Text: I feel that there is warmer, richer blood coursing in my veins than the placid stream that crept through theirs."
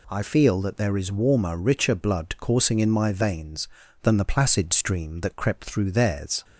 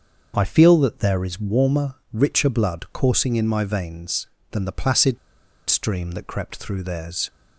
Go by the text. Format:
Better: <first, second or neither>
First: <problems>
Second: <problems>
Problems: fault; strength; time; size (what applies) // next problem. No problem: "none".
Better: first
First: none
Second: starts louder than the rest; until 1.3 s; 6.5 dB // pauses between "placid" and "stream"; noticeable; at 5.1 s; 0.52 s long